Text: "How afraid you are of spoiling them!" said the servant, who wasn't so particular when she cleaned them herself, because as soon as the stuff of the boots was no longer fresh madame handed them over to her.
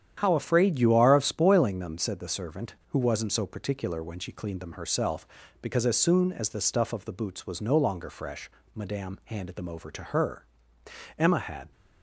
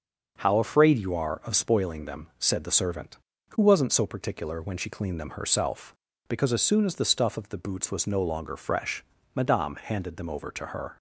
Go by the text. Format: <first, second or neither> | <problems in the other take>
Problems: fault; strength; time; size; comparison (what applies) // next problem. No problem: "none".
second | starts louder than the rest; strong; until 1.1 s; 9 dB; also in the second // pauses between "fresh" and "madame"; slight; at 8.4 s; 0.28 s long; slight in the second // goes on to say "Emma had"; from 11.1 s on; 0.54 s long